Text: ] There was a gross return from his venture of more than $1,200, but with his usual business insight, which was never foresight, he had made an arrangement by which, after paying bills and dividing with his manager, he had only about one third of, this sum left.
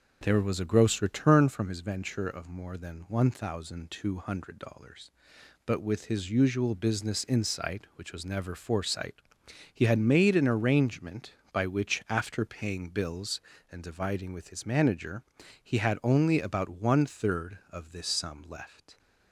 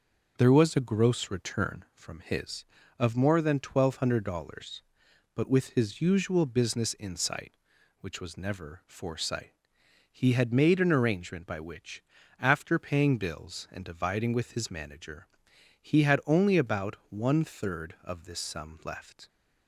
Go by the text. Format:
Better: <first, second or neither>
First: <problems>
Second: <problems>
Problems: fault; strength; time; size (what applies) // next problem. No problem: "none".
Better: first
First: none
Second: starts louder than the rest; noticeable; until 1.3 s; 6 dB // skips "venture"; at 2.8 s